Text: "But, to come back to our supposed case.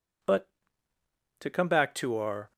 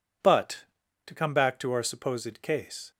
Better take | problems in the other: second | stops before "supposed case"; at 2.5 s

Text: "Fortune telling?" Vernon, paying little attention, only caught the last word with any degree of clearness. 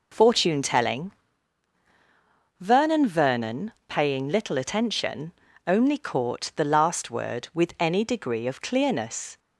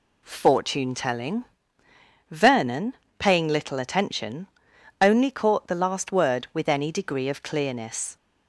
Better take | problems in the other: second | says "Vernon" twice; at 3.0 s

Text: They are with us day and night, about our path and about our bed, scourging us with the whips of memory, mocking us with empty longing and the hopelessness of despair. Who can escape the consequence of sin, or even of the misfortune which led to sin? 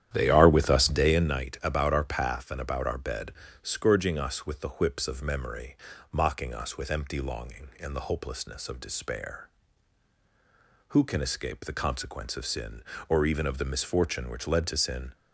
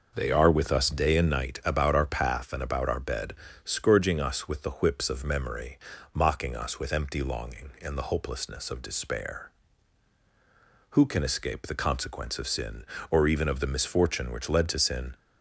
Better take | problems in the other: second | starts louder than the rest; strong; until 1.2 s; 10.5 dB

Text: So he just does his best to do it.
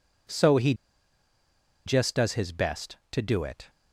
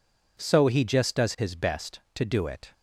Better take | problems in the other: second | pauses between "he" and "just"; at 0.7 s; 1.1 s long

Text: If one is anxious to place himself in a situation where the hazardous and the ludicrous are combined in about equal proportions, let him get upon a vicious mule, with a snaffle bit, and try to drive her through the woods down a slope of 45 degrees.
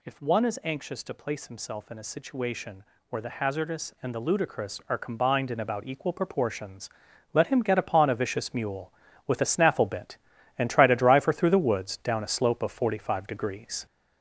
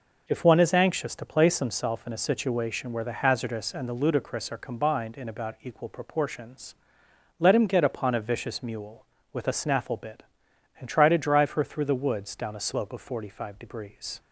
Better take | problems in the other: second | gets louder; noticeable; throughout; 5 dB // pauses between "situation" and "where"; slight; at 2.8 s; 0.26 s long

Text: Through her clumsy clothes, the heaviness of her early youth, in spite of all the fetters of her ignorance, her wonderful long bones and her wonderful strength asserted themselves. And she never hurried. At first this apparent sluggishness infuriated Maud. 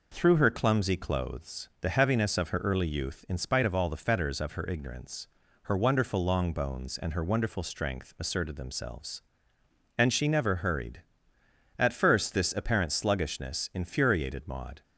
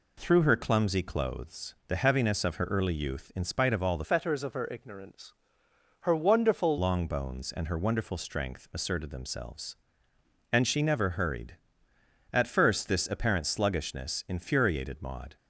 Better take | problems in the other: first | changes voice from "fetters" to "wonderful"; from 4.0 to 6.7 s; 2.7 s long

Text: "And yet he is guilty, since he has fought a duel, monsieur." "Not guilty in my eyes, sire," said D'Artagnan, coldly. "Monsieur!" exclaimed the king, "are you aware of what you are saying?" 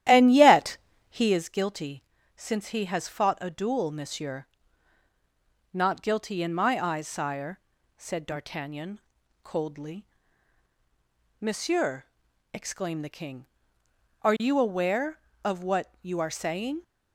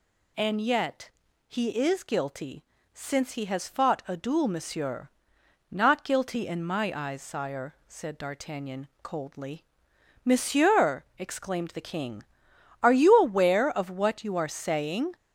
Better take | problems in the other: second | starts louder than the rest; strong; until 1.5 s; 12 dB // pauses between "yet" and "he"; slight; at 0.7 s; 0.32 s long; slight in the second

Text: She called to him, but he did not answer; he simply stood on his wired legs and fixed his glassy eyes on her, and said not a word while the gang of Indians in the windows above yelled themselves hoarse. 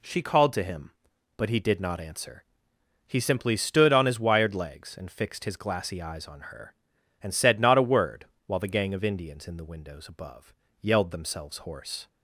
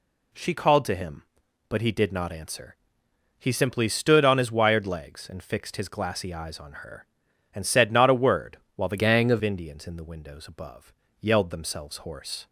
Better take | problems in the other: first | pauses between "word" and "while"; slight; at 8.5 s; 0.18 s long; slight in the first // changes voice from "gang" to "of"; from 8.9 to 9.4 s; 0.5 s long // pauses between "above" and "yelled"; slight; at 10.9 s; 0.30 s long; slight in the first

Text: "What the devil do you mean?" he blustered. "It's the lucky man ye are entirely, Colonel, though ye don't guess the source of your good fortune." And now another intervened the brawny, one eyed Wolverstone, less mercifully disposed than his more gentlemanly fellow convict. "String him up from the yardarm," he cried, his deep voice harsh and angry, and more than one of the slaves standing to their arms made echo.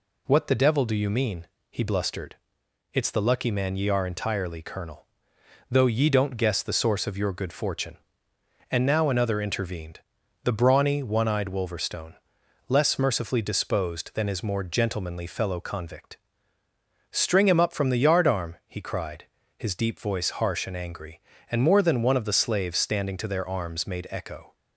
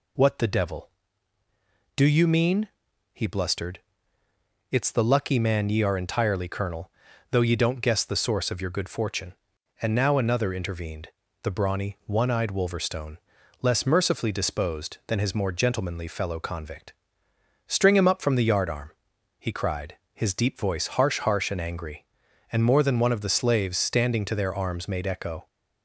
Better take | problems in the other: first | pauses between "intervened" and "the"; slight; at 11.0 s; 0.34 s long; also in the first // says "harsh" twice; at 21.1 s

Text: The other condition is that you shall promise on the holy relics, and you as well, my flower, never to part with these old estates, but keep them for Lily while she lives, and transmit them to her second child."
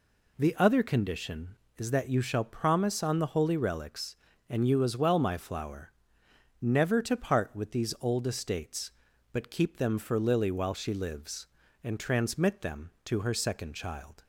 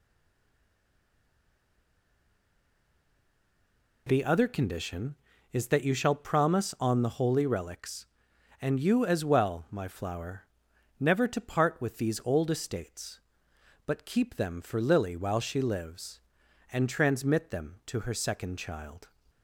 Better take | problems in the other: first | stays silent before the first word; strong; until 4.0 s; 4.0 s long

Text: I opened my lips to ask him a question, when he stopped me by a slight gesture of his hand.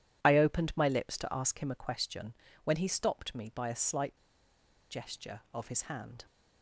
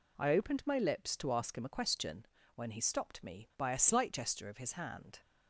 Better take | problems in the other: second | pauses between "slight" and "gesture"; noticeable; at 4.1 s; 0.73 s long

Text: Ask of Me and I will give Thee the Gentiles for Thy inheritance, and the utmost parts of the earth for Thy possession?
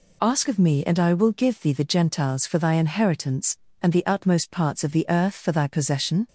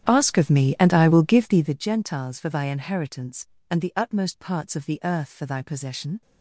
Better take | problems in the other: first | starts louder than the rest; strong; until 1.9 s; 10 dB

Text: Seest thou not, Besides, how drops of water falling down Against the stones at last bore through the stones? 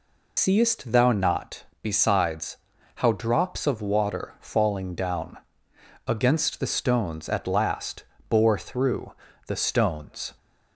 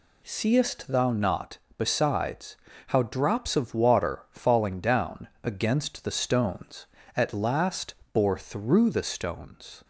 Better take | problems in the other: second | loses the start of "Seest"; at 0.3 s; 95 ms // pauses between "down" and "Against"; noticeable; at 5.3 s; 0.70 s long // pauses between "last" and "bore"; slight; at 8.0 s; 0.22 s long; slight in the second // pauses between "through" and "the"; slight; at 9.1 s; 0.32 s long

